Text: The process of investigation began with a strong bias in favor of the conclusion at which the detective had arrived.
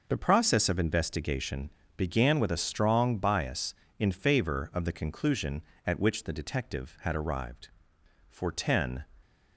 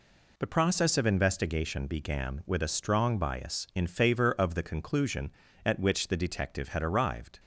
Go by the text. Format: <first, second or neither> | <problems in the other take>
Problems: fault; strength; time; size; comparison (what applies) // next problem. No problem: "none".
second | pauses between "investigation" and "began"; slight; at 1.6 s; 0.28 s long // goes on to say "For ten"; noticeable; from 8.2 s on; 0.76 s long